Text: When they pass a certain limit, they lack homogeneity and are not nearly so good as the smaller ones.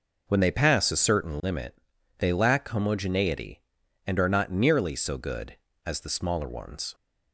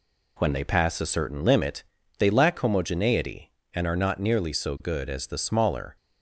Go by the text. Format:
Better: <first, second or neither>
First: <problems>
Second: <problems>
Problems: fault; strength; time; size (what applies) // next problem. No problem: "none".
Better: first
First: none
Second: stops before "ones"; at 5.9 s